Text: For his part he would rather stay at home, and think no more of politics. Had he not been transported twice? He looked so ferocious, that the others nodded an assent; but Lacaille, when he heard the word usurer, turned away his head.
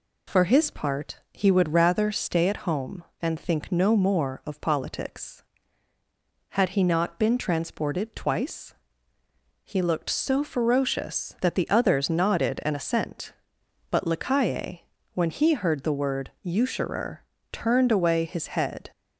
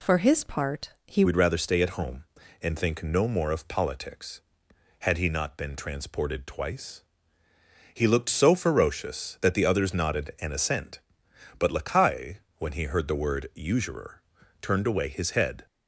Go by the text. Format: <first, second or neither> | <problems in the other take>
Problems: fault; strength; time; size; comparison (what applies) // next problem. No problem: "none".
first | changes voice at "would"; from 1.2 s on; 14.4 s long